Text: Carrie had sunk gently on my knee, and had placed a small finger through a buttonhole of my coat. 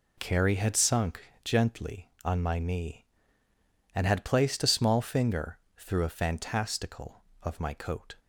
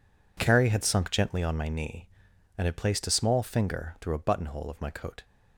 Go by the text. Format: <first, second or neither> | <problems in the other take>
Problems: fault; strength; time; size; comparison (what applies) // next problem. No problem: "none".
second | pauses between "sunk" and "gently"; slight; at 1.2 s; 0.24 s long // pauses between "finger" and "through"; slight; at 5.5 s; 0.18 s long // says "fantastical" for "buttonhole"; at 6.1 s